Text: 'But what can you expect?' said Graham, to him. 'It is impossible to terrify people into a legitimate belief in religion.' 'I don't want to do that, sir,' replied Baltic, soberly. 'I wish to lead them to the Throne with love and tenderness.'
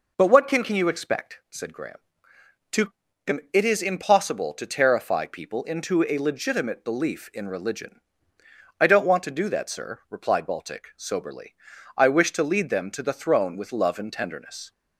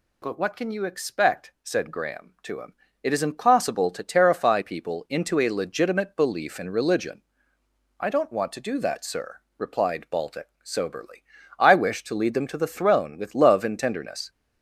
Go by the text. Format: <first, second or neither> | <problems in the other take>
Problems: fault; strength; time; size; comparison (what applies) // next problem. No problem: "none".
second | says "can" twice; at 0.6 s // pauses between "to" and "him"; slight; at 2.9 s; 0.34 s long